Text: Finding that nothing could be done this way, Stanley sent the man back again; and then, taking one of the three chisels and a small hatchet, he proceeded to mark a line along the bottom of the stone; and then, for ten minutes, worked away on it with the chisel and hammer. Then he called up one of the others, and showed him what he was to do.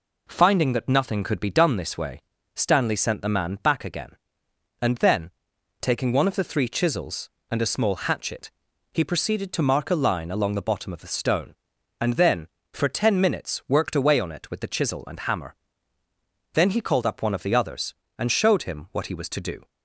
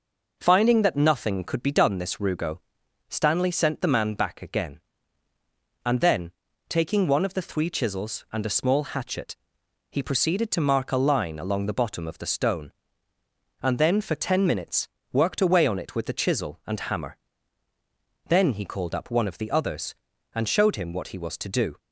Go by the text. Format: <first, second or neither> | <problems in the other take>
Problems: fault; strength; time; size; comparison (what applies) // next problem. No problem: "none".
first | says "rugo" for "way"; at 2.1 s